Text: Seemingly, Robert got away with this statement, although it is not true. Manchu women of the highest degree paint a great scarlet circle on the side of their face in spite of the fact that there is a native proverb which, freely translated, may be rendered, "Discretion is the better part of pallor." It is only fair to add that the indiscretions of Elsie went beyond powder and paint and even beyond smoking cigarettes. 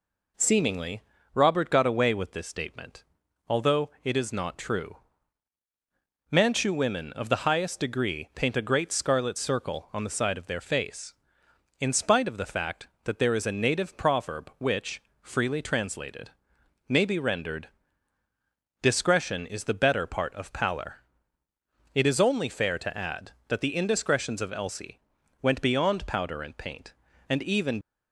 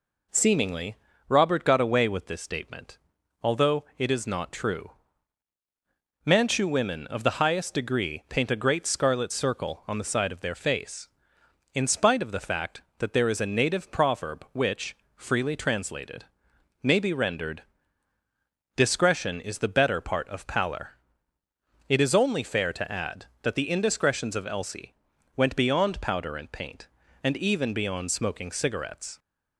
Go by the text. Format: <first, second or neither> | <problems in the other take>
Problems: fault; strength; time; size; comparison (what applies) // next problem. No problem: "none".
second | pauses between "Elsie" and "went"; at 25.0 s; 0.42 s long; also in the second // stops before "beyond smoking cigarettes"; at 27.8 s